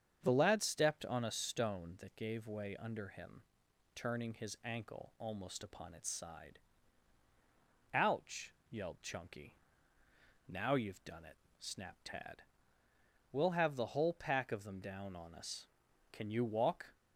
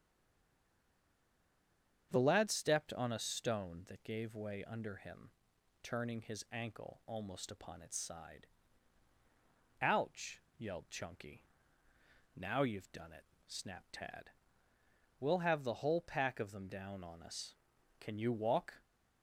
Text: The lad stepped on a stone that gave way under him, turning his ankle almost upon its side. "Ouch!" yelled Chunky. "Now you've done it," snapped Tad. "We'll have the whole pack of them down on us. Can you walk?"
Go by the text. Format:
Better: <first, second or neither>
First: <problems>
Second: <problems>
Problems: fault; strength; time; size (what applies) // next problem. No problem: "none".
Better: first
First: starts louder than the rest; strong; until 1.2 s; 8 dB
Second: stays silent before the first word; noticeable; until 2.1 s; 2.1 s long // starts louder than the rest; strong; until 3.1 s; 8 dB